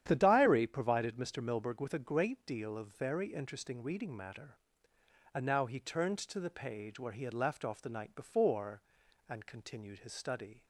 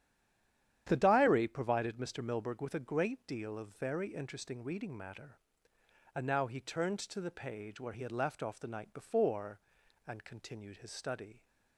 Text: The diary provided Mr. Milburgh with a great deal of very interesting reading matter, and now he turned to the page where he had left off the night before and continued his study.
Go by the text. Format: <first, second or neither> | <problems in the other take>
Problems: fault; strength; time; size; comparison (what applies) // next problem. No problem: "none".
first | stays silent before the first word; slight; until 0.8 s; 0.8 s long // starts louder than the rest; strong; until 1.8 s; 10 dB; strong in the first